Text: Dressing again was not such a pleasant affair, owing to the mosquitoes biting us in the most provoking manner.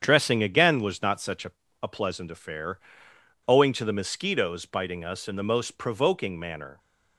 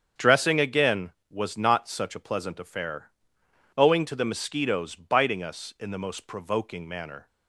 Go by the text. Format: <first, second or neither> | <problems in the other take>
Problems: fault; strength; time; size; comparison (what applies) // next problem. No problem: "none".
second | starts louder than the rest; strong; until 1.0 s; 8 dB; strong in the second // says "a" twice; at 1.8 s